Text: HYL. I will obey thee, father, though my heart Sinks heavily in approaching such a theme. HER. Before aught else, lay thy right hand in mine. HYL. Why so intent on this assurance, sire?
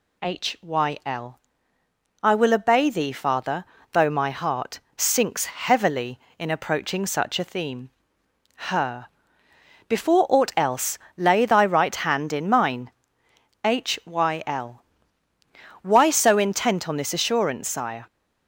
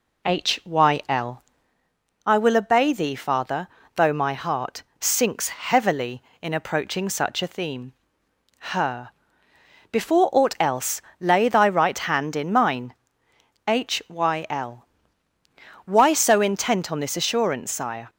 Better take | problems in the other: first | starts louder than the rest; slight; until 1.7 s; 2 dB // pauses between "heart" and "Sinks"; slight; at 4.8 s; 0.18 s long; slight in the first

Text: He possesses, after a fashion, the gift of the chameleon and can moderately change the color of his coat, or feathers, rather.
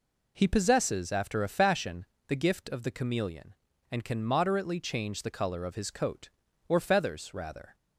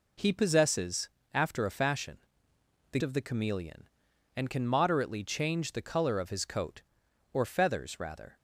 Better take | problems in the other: first | skips "gift"; at 3.0 s

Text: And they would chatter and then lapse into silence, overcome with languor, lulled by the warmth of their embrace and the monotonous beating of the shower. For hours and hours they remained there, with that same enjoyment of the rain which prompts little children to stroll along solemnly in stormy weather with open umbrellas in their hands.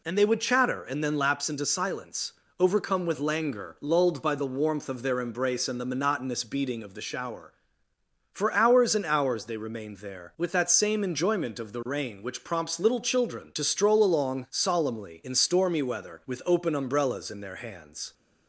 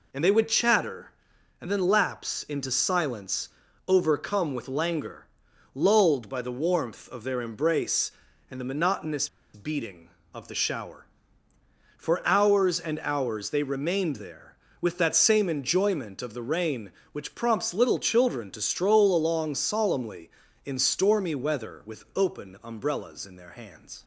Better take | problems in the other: first | pauses between "monotonous" and "beating"; slight; at 9.2 s; 0.26 s long

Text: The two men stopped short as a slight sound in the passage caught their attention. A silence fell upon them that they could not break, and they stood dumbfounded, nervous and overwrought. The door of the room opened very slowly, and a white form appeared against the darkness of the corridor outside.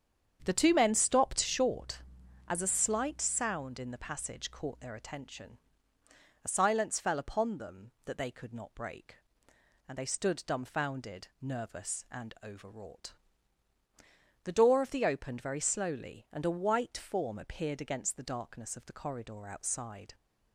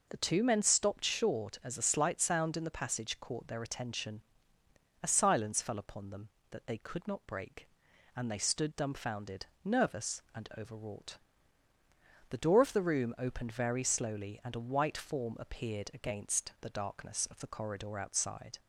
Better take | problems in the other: second | starts louder than the rest; strong; until 1.4 s; 8 dB // skips "room"; at 15.0 s

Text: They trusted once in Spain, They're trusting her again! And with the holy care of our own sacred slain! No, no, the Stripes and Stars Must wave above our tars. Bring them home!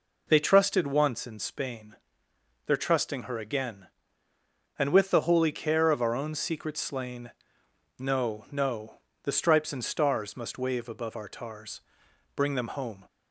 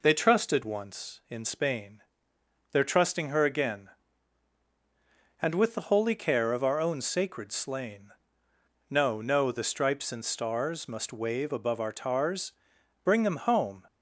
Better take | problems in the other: second | says "secret" for "sacred"; at 6.3 s

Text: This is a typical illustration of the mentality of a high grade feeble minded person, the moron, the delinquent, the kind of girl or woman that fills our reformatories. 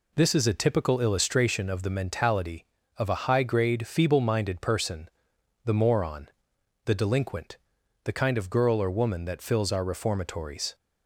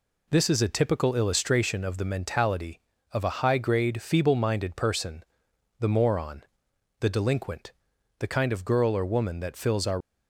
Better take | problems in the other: first | stops before "reformatories"; at 9.9 s

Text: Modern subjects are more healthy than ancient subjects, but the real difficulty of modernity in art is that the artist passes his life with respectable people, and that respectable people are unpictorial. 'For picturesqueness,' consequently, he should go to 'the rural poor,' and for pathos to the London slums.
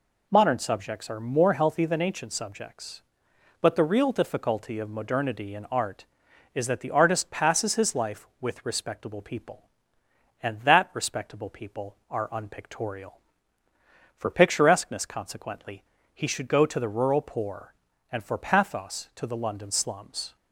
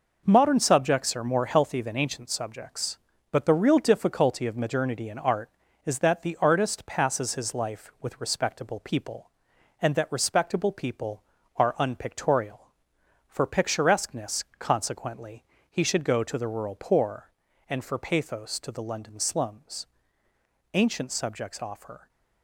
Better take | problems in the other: first | goes on to say "Ancient subjects offer"; from 20.7 s on; 1.3 s long

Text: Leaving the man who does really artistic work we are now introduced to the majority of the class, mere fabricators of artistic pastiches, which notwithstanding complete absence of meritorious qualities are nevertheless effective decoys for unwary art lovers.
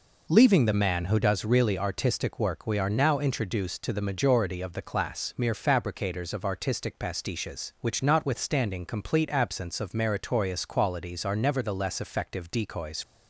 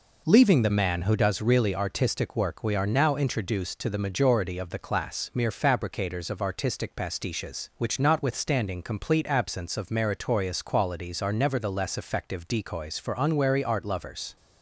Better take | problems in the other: second | stops before "for unwary art lovers"; at 13.0 s

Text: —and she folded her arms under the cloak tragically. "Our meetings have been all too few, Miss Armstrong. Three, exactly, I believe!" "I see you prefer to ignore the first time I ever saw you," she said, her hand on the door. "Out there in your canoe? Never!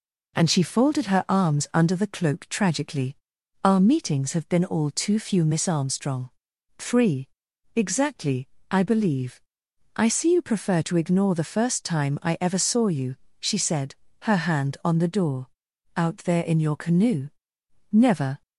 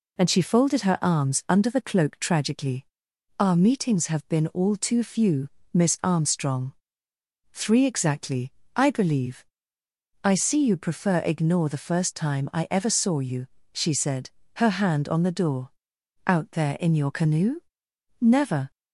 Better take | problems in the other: first | skips "to"; at 11.2 s

